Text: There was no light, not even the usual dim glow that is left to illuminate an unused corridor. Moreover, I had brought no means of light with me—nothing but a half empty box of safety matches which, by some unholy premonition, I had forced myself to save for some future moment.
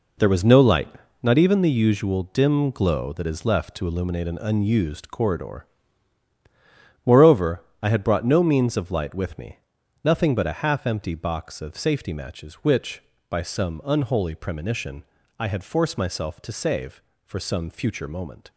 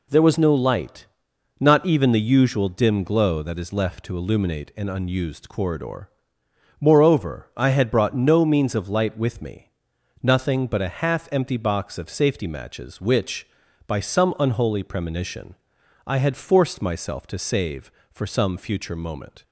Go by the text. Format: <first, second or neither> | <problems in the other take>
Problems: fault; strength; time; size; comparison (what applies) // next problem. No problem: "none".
second | gets quieter; strong; throughout; 11.5 dB